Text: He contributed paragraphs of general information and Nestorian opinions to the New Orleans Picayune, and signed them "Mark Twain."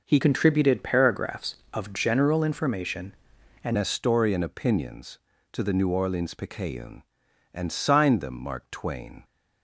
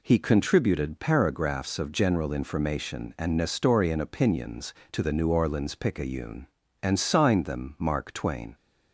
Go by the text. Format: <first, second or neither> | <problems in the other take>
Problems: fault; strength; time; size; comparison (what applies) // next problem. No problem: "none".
second | changes voice from "contributed" to "and"; from 0.2 to 3.7 s; 3.5 s long